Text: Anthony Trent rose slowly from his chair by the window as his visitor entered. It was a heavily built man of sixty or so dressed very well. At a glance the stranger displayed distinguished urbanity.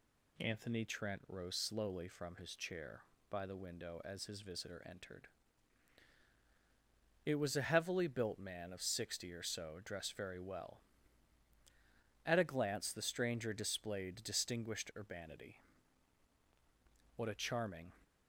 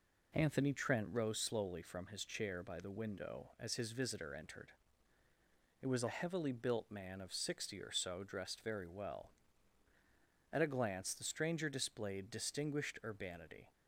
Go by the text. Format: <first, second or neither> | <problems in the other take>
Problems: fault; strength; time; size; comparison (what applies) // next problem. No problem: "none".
second | goes on to say "What a charming"; noticeable; from 17.1 s on; 0.74 s long